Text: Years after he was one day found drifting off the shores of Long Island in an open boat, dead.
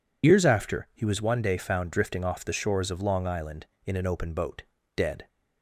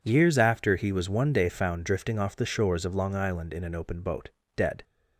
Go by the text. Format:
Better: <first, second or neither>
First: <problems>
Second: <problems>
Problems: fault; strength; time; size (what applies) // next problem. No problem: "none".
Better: second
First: loses the start of "Years"; at 0.2 s; 45 ms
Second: none